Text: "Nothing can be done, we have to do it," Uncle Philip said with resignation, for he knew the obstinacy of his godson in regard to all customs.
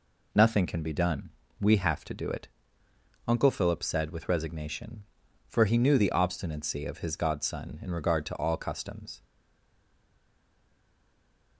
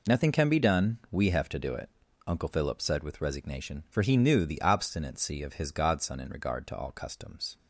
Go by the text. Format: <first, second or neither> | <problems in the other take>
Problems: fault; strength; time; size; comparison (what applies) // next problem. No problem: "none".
second | stays silent after the last word; from 9.2 s on; 2.3 s long